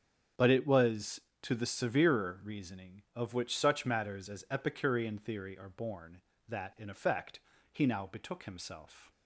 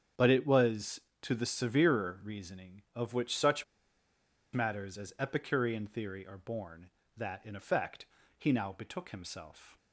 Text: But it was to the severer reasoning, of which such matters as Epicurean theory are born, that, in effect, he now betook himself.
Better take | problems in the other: first | starts louder than the rest; strong; until 1.4 s; 8 dB; strong in the first // pauses between "such" and "matters"; noticeable; at 3.6 s; 0.89 s long

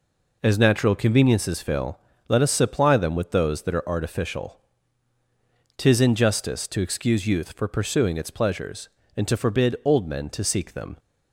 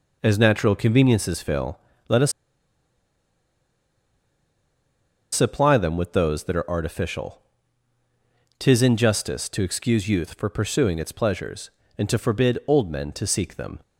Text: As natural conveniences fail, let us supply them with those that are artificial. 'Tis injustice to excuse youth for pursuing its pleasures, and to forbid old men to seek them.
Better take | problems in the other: first | pauses between "us" and "supply"; strong; at 2.3 s; 3.0 s long

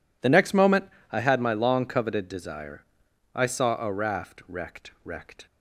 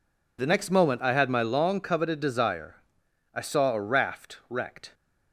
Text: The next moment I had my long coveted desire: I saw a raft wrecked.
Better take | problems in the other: second | pauses between "moment" and "I"; slight; at 0.8 s; 0.26 s long // says "wrecked" twice; at 5.0 s

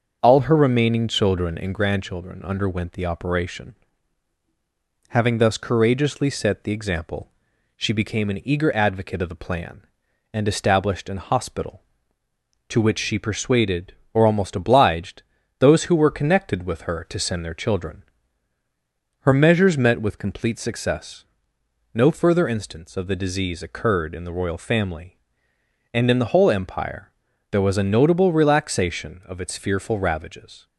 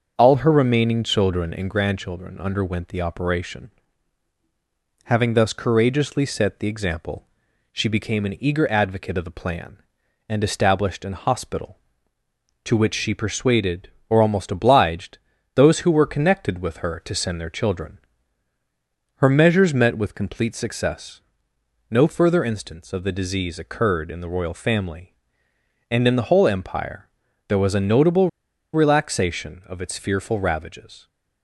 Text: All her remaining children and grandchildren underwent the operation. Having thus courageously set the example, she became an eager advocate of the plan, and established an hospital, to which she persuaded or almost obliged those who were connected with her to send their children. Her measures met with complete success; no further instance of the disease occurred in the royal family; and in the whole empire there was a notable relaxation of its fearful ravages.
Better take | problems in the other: first | starts louder than the rest; until 1.1 s; 6.5 dB; also in the first // pauses between "obliged" and "those"; slight; at 15.1 s; 0.36 s long; slight in the first // pauses between "empire" and "there"; at 27.0 s; 0.40 s long; also in the first // pauses between "notable" and "relaxation"; at 28.2 s; 0.45 s long

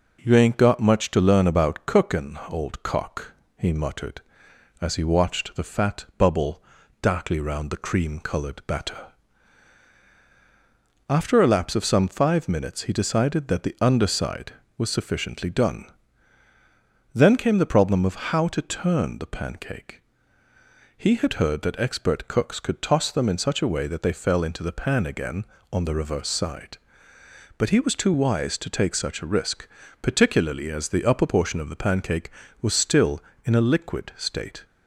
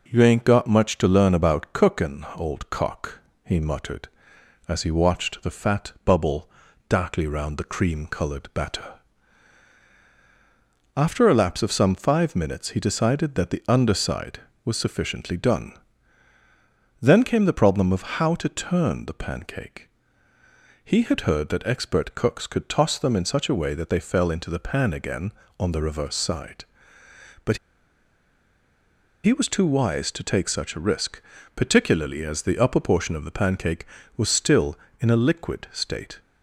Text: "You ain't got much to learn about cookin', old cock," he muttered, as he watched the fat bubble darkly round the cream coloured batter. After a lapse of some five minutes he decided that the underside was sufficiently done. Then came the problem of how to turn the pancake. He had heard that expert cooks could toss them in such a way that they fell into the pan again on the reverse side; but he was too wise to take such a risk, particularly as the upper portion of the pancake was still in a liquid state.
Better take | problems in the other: first | pauses between "bubble" and "darkly"; at 6.4 s; 0.38 s long; also in the first // pauses between "but" and "he"; strong; at 27.5 s; 1.6 s long

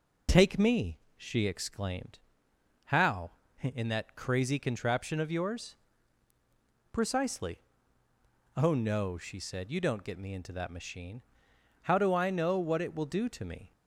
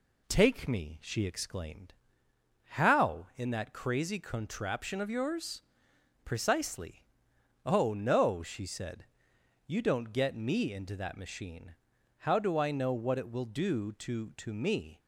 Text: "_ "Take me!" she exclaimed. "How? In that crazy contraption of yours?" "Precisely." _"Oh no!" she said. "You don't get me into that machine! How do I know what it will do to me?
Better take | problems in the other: first | says "to" twice; at 14.3 s

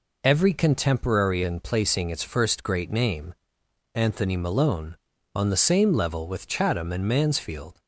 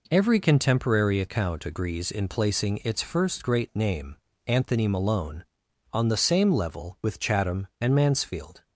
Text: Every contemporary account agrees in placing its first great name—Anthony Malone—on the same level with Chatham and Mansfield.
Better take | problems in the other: second | skips "account agrees"; at 1.4 s

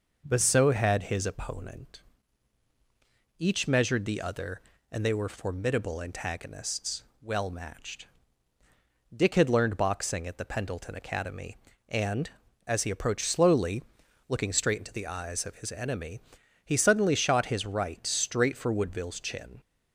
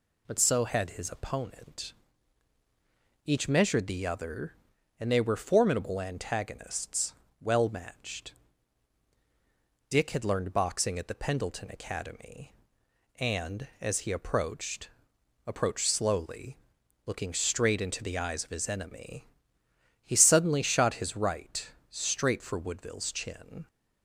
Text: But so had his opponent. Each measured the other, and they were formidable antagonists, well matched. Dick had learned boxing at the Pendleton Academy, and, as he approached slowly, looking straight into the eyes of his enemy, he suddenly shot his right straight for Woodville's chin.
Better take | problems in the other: first | says "approached" twice; at 15.4 s // pauses between "right" and "straight"; slight; at 21.6 s; 0.22 s long

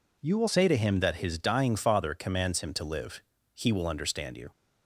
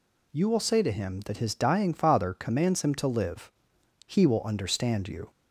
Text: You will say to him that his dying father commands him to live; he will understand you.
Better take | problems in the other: second | changes voice at "say"; from 0.4 s on; 4.1 s long

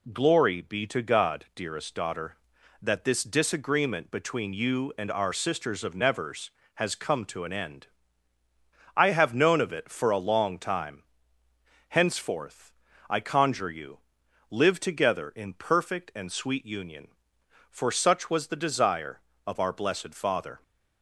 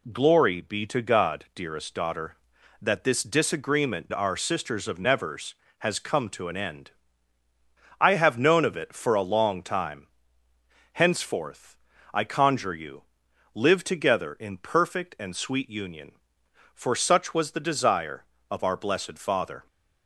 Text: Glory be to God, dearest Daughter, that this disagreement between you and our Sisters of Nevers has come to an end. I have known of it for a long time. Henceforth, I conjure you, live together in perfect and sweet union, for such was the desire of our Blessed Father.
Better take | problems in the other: first | skips "between you and"; at 4.1 s

